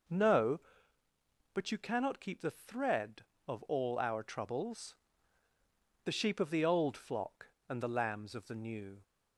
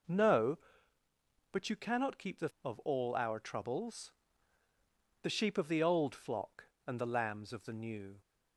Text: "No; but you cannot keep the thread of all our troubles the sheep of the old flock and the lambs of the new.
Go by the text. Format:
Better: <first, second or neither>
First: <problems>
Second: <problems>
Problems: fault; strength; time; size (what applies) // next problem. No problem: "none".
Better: first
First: pauses between "troubles" and "the"; at 4.9 s; 1.0 s long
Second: skips "thread"; at 2.5 s // pauses between "troubles" and "the"; at 4.1 s; 1.1 s long